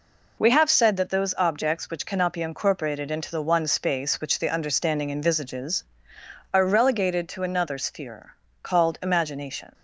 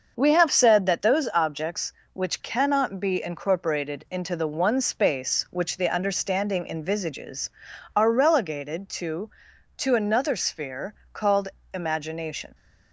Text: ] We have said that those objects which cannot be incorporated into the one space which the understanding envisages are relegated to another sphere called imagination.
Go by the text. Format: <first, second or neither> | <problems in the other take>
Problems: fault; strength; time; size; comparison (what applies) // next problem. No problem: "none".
first | starts louder than the rest; until 1.1 s; 6.5 dB // says "to" twice; at 9.7 s // pauses between "sphere" and "called"; slight; at 10.9 s; 0.18 s long; slight in the first // pauses between "called" and "imagination"; slight; at 11.4 s; 0.26 s long